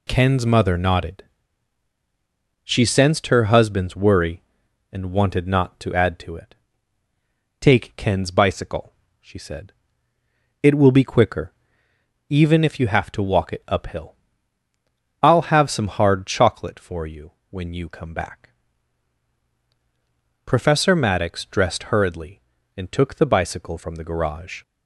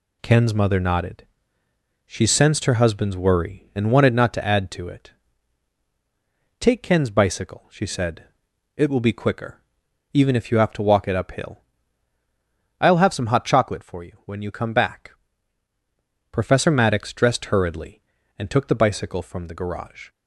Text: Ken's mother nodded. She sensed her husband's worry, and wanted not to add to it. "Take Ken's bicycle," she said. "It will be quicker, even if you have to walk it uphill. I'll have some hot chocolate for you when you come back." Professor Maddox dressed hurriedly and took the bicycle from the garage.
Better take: second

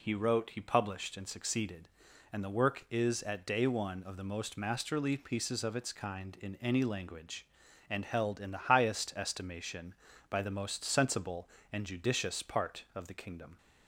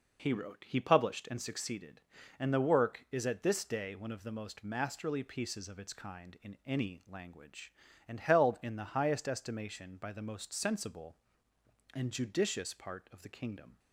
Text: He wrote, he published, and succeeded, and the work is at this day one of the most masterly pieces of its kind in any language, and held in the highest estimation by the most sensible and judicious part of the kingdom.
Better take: second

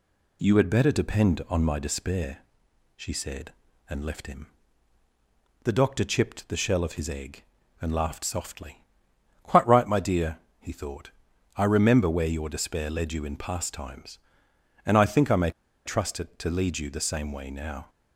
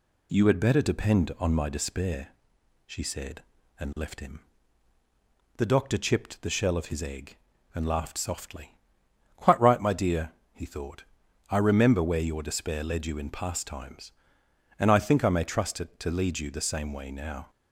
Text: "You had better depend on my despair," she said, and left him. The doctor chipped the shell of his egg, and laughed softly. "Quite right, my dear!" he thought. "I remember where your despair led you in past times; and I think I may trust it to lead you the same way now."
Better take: second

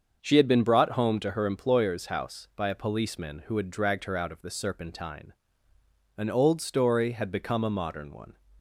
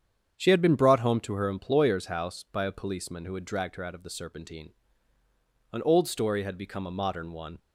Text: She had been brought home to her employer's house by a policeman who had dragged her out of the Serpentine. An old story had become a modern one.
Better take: neither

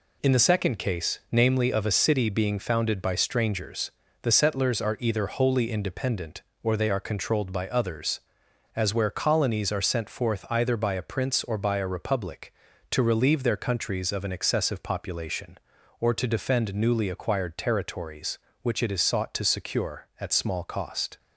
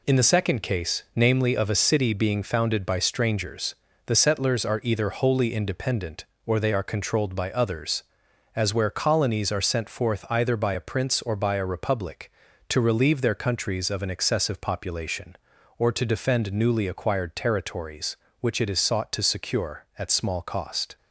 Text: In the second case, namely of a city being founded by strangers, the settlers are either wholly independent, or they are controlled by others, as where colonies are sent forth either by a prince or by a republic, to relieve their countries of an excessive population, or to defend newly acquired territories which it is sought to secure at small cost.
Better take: neither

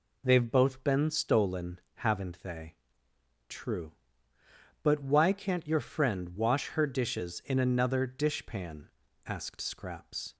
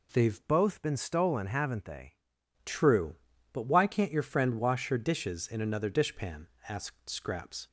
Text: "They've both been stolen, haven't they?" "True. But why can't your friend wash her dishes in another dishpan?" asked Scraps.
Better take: first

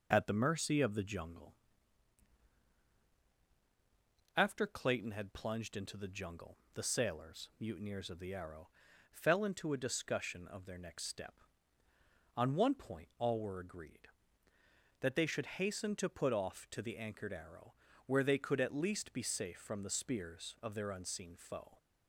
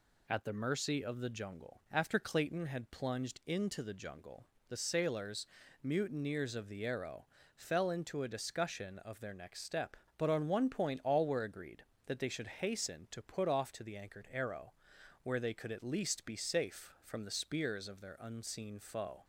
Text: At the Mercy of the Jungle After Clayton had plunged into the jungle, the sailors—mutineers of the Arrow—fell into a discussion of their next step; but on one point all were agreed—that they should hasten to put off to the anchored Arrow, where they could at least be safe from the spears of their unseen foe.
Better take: second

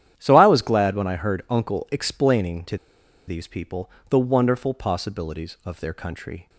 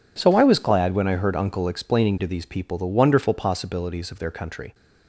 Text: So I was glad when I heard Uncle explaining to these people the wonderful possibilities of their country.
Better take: second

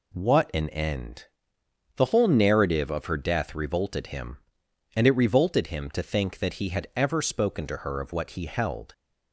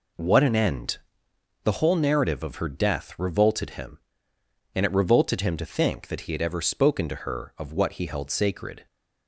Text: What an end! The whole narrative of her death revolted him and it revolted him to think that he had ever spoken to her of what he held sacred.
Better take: second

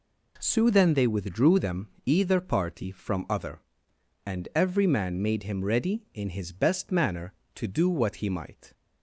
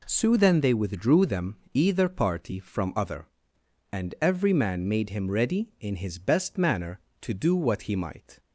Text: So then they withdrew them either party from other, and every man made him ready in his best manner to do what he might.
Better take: neither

